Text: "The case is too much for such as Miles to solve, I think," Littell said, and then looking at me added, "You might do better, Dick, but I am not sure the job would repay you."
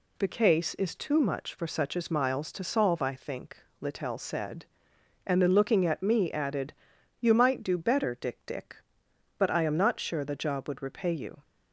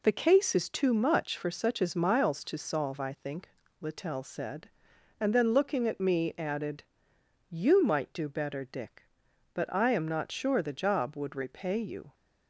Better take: second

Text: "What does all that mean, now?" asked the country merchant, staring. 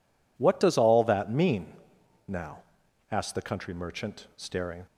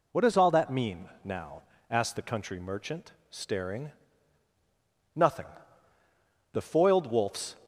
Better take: first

